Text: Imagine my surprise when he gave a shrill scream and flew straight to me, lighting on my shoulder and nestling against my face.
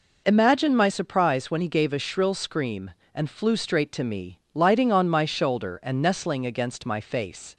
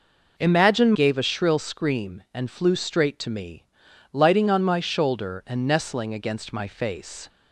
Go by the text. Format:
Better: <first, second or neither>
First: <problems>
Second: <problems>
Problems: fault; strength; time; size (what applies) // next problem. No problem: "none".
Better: first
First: none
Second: skips "my surprise when he"; at 0.9 s